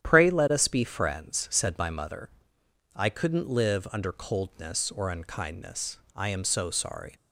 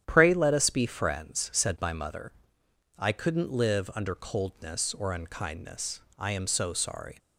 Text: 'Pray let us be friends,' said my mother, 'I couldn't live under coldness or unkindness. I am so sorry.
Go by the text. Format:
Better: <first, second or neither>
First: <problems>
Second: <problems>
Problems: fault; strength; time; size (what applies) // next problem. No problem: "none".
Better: neither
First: starts louder than the rest; strong; until 1.0 s; 10 dB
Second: starts louder than the rest; strong; until 1.0 s; 10.5 dB